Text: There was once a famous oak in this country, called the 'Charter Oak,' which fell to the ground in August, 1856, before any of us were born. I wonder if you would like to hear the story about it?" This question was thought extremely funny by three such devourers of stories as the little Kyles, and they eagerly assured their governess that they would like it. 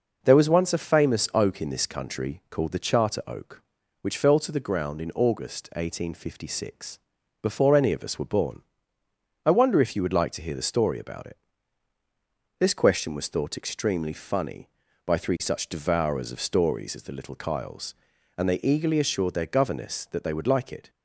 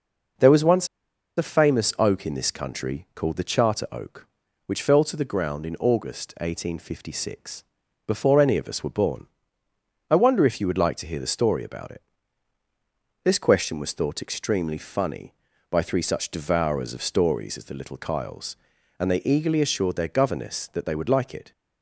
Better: first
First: none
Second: pauses between "once" and "a"; noticeable; at 0.8 s; 0.51 s long

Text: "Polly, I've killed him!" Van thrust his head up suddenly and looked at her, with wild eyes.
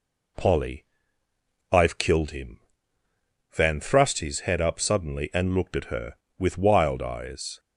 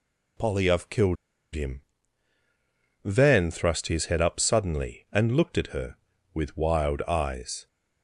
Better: first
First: none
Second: pauses between "killed" and "him"; at 1.1 s; 0.38 s long

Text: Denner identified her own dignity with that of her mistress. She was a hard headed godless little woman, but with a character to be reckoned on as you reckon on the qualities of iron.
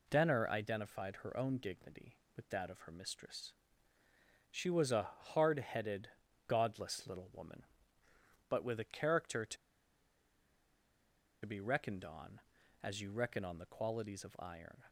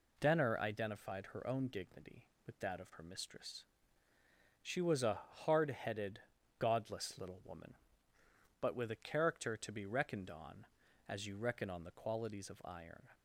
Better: second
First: pauses between "a" and "hard"; slight; at 5.0 s; 0.26 s long // pauses between "headed" and "godless"; at 6.0 s; 0.40 s long // pauses between "to" and "be"; strong; at 9.5 s; 1.8 s long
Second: pauses between "a" and "hard"; slight; at 5.1 s; 0.26 s long // pauses between "headed" and "godless"; at 6.1 s; 0.40 s long

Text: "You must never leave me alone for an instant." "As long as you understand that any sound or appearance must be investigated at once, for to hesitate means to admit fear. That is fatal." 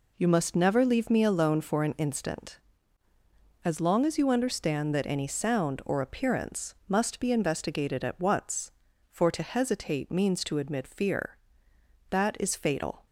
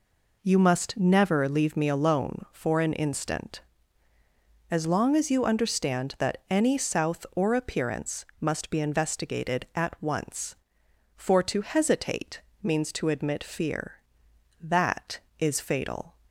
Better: first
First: none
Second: says "south" for "sound"; at 6.7 s // pauses between "hesitate" and "means"; slight; at 12.4 s; 0.22 s long

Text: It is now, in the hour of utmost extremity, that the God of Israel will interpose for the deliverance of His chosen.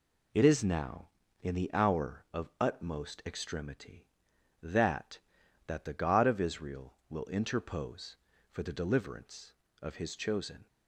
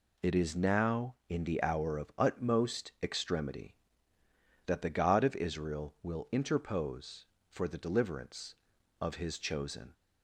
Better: second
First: says "that" twice; at 5.6 s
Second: none

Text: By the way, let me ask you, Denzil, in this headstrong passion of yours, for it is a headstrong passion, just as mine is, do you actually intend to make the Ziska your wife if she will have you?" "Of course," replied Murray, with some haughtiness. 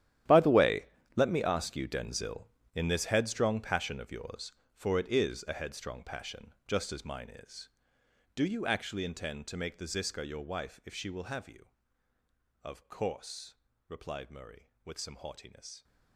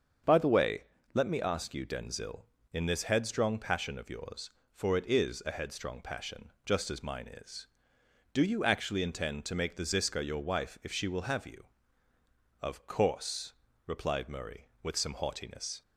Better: second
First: gets quieter; strong; throughout; 16.5 dB // starts louder than the rest; strong; until 1.5 s; 12 dB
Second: starts louder than the rest; strong; until 1.5 s; 7 dB

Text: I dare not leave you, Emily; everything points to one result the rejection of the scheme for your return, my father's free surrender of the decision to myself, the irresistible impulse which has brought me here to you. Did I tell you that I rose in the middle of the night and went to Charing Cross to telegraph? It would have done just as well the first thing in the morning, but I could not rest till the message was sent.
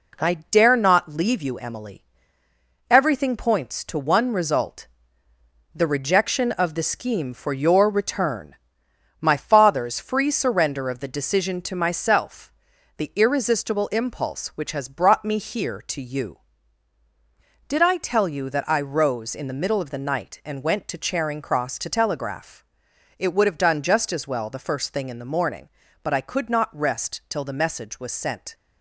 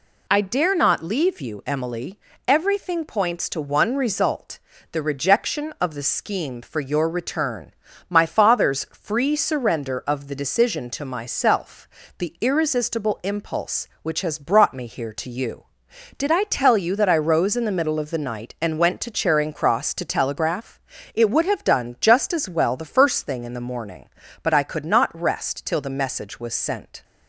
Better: second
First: gets quieter; noticeable; throughout; 5.5 dB // pauses between "I" and "dare"; slight; at 0.3 s; 0.16 s long // pauses between "result" and "the"; noticeable; at 4.8 s; 0.90 s long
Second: pauses between "result" and "the"; slight; at 4.5 s; 0.32 s long

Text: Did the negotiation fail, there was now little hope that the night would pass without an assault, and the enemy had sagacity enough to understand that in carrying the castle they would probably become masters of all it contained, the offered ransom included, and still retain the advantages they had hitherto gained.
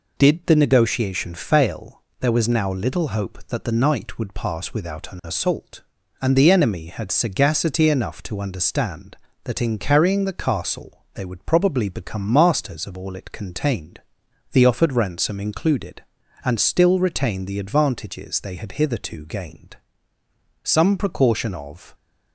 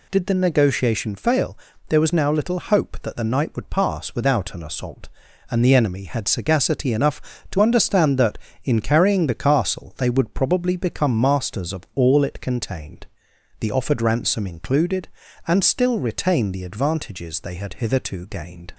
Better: second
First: goes on to say "Some precaution of"; from 20.6 s on; 1.3 s long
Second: none

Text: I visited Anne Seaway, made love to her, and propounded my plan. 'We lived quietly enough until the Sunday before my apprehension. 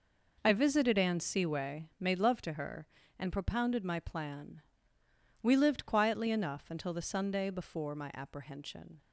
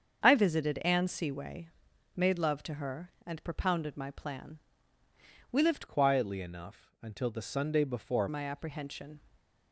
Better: first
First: none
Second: starts louder than the rest; strong; until 1.2 s; 7 dB // changes voice from "quietly" to "before"; from 5.8 to 8.2 s; 2.4 s long // stays silent after the last word; slight; from 9.1 s on; 0.6 s long

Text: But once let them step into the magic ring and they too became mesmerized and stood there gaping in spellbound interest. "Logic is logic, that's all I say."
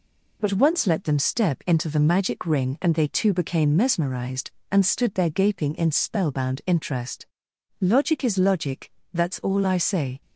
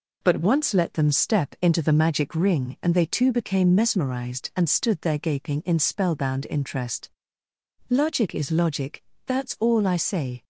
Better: neither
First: none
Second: none

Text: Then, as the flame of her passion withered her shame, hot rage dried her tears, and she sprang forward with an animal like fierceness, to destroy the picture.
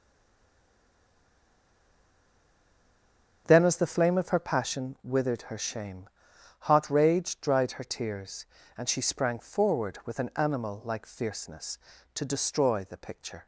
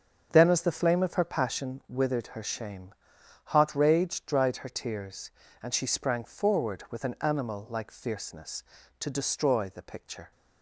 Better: second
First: stays silent before the first word; strong; until 3.4 s; 3.4 s long // starts louder than the rest; strong; until 4.4 s; 7 dB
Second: starts louder than the rest; strong; until 1.3 s; 7 dB

